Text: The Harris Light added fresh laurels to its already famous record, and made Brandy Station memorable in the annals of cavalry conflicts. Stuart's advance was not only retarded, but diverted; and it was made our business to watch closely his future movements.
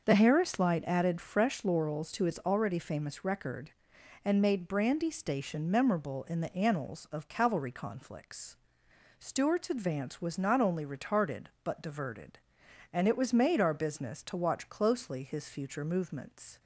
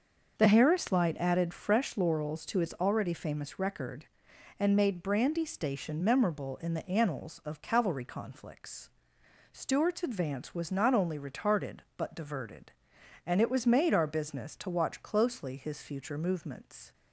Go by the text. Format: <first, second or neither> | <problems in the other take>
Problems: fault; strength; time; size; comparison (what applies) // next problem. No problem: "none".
neither | starts louder than the rest; the same in both